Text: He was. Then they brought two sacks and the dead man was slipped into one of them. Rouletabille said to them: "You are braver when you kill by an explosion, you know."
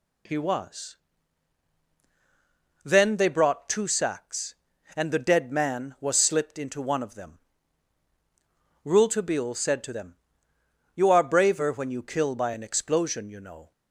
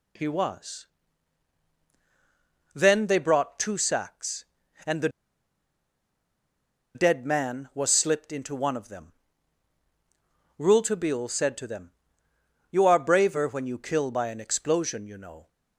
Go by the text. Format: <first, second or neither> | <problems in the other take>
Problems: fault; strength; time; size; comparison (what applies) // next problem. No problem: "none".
first | pauses between "the" and "dead"; strong; at 5.0 s; 1.8 s long